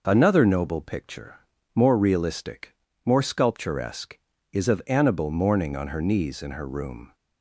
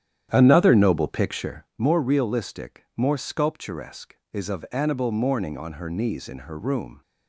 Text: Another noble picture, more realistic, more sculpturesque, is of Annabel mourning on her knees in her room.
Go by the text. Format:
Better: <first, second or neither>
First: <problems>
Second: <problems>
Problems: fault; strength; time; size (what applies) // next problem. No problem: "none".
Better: first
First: none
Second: starts louder than the rest; strong; until 1.7 s; 10 dB